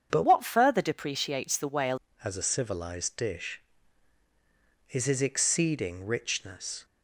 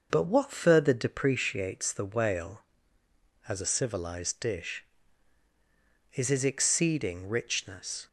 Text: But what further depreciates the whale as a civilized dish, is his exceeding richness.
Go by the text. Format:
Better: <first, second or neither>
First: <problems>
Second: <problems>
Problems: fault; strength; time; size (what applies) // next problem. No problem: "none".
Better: second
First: starts louder than the rest; strong; until 1.1 s; 7.5 dB // changes voice from "what" to "whale"; from 0.2 to 1.9 s; 1.7 s long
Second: starts louder than the rest; noticeable; until 1.1 s; 6 dB